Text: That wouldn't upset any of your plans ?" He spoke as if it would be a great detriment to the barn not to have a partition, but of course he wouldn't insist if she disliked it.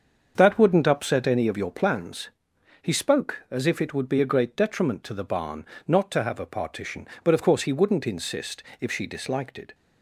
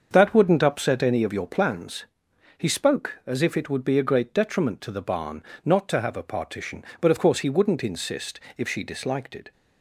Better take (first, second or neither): neither